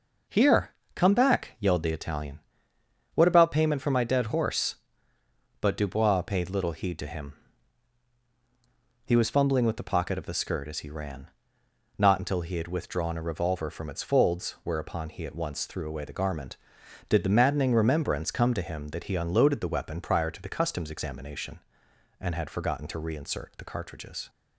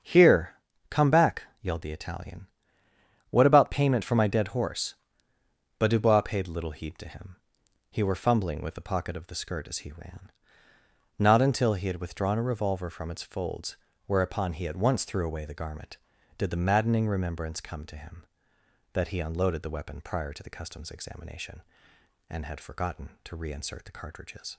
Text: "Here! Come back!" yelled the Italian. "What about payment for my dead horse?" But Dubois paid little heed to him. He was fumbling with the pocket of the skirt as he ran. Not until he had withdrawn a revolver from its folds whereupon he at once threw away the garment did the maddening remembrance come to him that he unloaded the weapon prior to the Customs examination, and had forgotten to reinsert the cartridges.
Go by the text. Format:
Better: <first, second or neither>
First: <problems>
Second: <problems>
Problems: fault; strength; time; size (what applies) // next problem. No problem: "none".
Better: first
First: none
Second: starts louder than the rest; until 1.3 s; 7 dB // says "were" for "was"; at 8.0 s // pauses between "folds" and "whereupon"; slight; at 13.7 s; 0.30 s long